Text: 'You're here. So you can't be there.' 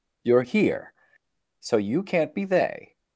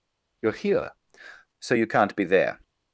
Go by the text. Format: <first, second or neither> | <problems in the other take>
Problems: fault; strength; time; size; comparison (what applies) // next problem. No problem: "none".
second | says "they" for "there"; at 2.4 s